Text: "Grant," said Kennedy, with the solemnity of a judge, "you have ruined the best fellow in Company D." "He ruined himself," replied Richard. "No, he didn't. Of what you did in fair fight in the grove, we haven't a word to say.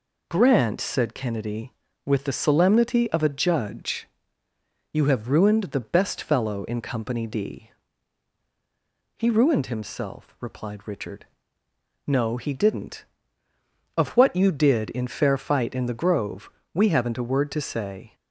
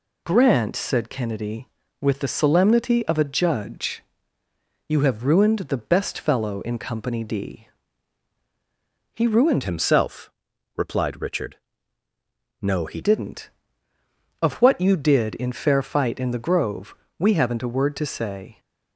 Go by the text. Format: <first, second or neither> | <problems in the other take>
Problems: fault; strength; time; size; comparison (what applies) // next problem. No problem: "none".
first | changes voice from "himself" to "he"; from 9.6 to 13.0 s; 3.4 s long